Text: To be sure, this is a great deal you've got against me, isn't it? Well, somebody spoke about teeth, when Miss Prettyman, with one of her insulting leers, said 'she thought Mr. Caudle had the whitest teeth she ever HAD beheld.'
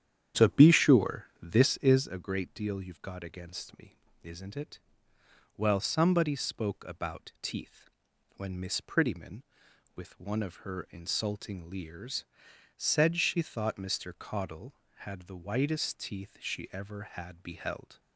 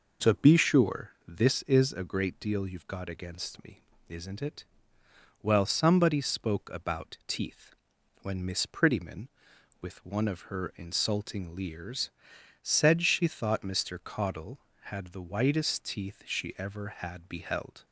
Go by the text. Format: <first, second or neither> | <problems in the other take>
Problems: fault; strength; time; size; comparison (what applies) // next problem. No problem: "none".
second | starts louder than the rest; strong; until 2.1 s; 9.5 dB